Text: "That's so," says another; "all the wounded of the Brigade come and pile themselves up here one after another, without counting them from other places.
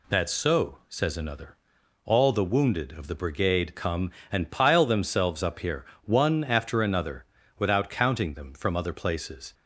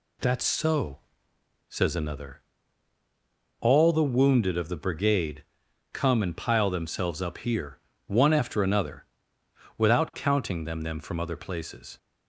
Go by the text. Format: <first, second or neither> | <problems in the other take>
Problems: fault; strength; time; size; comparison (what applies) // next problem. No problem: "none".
first | pauses between "Brigade" and "come"; noticeable; at 5.4 s; 0.50 s long // pauses between "here" and "one"; slight; at 7.7 s; 0.28 s long; slight in the first // says "them" twice; at 10.8 s